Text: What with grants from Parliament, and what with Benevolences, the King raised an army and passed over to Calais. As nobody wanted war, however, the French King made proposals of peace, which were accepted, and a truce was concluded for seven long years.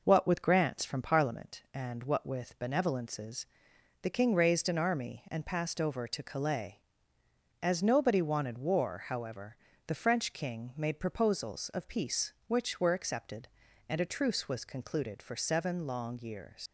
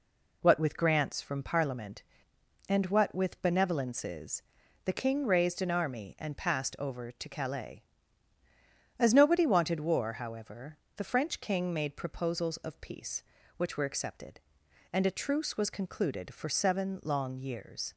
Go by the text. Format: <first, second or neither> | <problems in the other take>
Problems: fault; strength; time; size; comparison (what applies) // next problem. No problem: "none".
second | leaves "years" unfinished; at 16.6 s; 95 ms